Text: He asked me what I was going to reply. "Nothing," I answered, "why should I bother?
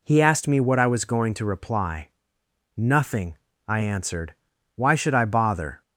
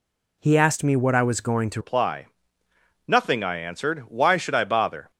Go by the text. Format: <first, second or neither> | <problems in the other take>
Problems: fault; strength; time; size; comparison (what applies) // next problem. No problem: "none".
first | changes voice at "reply"; from 1.8 s on; 3.3 s long